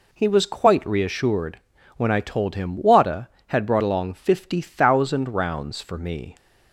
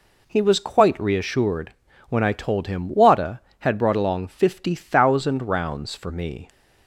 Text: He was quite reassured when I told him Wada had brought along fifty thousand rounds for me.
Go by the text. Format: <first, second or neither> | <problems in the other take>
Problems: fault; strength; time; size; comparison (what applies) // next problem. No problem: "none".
neither | pauses between "reassured" and "when"; the same in both